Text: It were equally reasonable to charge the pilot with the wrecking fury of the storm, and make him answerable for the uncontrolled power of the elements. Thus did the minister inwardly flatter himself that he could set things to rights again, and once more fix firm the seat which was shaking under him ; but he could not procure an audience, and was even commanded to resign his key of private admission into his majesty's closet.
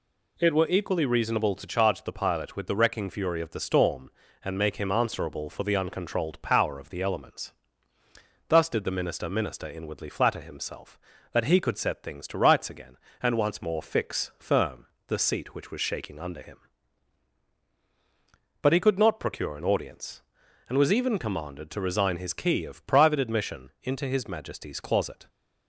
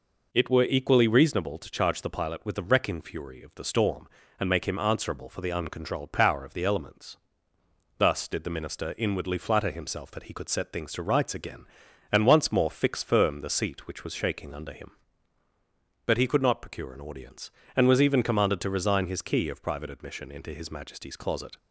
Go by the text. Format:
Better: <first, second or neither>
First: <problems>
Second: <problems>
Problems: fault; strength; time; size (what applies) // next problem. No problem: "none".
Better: second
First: says "minister" twice; at 9.2 s // pauses between "firm" and "the"; slight; at 14.8 s; 0.22 s long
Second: none